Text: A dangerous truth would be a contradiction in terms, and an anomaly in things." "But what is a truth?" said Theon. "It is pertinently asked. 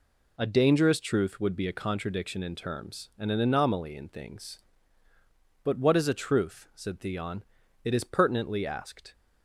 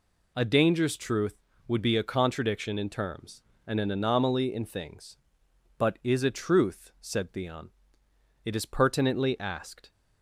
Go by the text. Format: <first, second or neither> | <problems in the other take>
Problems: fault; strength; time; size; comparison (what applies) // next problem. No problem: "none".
first | skips "what"; at 6.0 s